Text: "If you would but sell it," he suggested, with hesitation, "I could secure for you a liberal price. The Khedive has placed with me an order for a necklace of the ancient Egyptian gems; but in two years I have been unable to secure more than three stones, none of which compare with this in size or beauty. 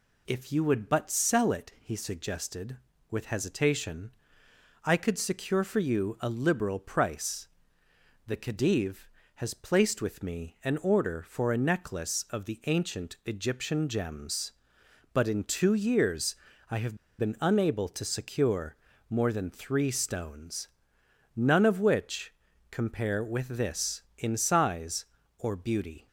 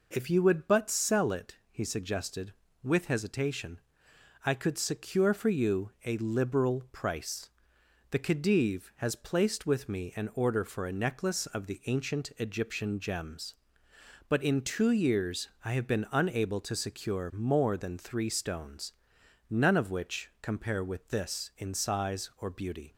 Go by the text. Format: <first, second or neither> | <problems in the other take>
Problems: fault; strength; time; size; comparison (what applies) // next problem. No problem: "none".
second | pauses between "years" and "I"; slight; at 16.3 s; 0.36 s long; slight in the second // pauses between "have" and "been"; slight; at 16.9 s; 0.21 s long // pauses between "secure" and "more"; slight; at 18.7 s; 0.32 s long // pauses between "which" and "compare"; at 22.3 s; 0.38 s long